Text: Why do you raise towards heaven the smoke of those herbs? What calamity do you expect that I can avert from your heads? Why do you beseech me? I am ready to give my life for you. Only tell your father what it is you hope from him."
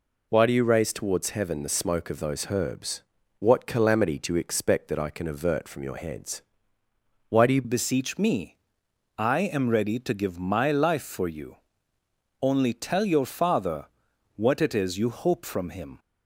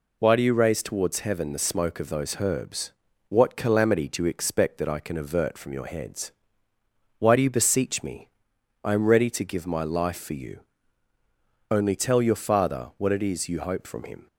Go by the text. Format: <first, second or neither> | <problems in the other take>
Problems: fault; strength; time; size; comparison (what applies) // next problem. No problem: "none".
second | changes voice at "beseech"; from 7.6 s on; 8.3 s long // pauses between "father" and "what"; noticeable; at 13.8 s; 0.50 s long